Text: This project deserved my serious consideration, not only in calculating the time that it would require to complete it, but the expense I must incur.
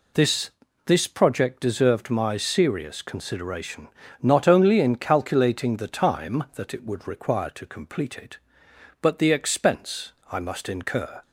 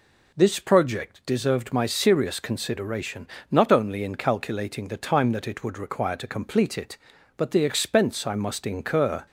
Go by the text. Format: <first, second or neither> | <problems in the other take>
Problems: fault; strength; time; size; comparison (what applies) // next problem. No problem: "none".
second | says "This" twice; at 0.8 s // pauses between "expense" and "I"; slight; at 10.1 s; 0.19 s long